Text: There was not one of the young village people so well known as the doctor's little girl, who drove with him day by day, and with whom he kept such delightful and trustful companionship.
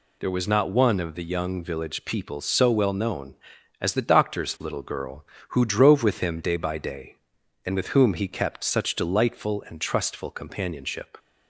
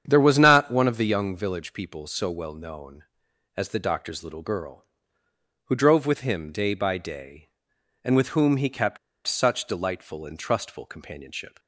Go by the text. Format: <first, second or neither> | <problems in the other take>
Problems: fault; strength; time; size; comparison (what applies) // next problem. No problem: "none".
first | starts louder than the rest; strong; until 1.0 s; 8.5 dB // pauses between "kept" and "such"; slight; at 8.9 s; 0.29 s long